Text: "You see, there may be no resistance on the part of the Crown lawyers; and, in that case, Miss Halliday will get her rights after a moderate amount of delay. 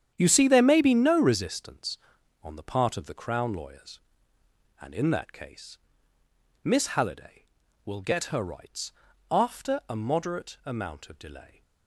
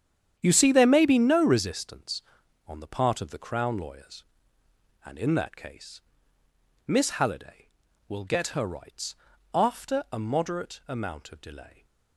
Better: neither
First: starts louder than the rest; strong; until 1.1 s; 9 dB // pauses between "rights" and "after"; at 8.9 s; 0.40 s long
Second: starts louder than the rest; strong; until 1.4 s; 9 dB // pauses between "rights" and "after"; at 9.1 s; 0.40 s long

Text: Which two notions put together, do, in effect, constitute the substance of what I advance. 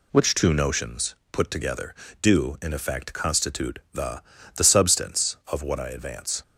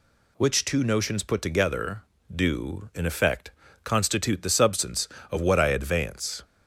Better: second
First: pauses between "notions" and "put"; slight; at 1.1 s; 0.16 s long // pauses between "constitute" and "the"; slight; at 3.7 s; 0.16 s long // says "the" twice; at 4.5 s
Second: none

